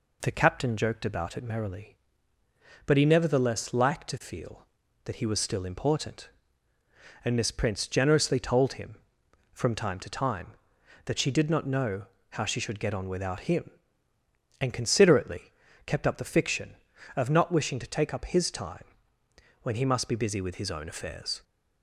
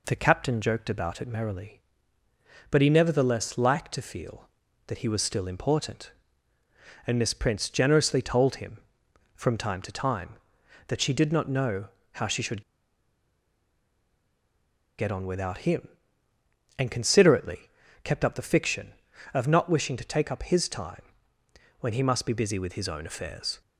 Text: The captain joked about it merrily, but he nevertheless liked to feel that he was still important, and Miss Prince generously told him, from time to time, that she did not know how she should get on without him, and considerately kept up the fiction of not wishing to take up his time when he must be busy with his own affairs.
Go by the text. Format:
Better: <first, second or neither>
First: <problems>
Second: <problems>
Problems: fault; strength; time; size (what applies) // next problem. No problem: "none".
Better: first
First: pauses between "know" and "how"; slight; at 12.0 s; 0.28 s long // pauses between "considerately" and "kept"; slight; at 15.5 s; 0.34 s long // pauses between "time" and "when"; noticeable; at 18.8 s; 0.78 s long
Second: pauses between "know" and "how"; slight; at 11.8 s; 0.28 s long // pauses between "should" and "get"; strong; at 12.6 s; 2.3 s long // pauses between "considerately" and "kept"; slight; at 17.6 s; 0.34 s long // pauses between "time" and "when"; noticeable; at 21.0 s; 0.78 s long